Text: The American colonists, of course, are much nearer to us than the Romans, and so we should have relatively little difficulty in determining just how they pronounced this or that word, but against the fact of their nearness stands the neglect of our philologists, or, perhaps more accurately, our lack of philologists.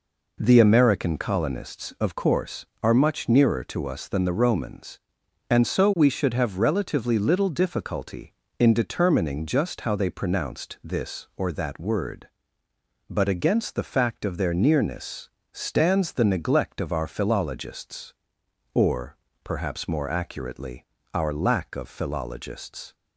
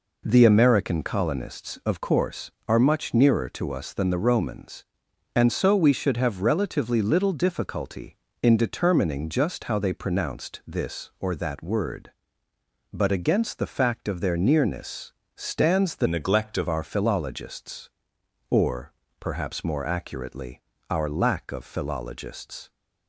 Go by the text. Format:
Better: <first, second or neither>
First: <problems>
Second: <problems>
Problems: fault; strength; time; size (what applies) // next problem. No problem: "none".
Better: first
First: pauses between "nearness" and "stands"; slight; at 15.2 s; 0.24 s long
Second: pauses between "nearness" and "stands"; slight; at 15.1 s; 0.24 s long // changes voice from "neglect" to "of"; from 16.0 to 16.6 s; 0.6 s long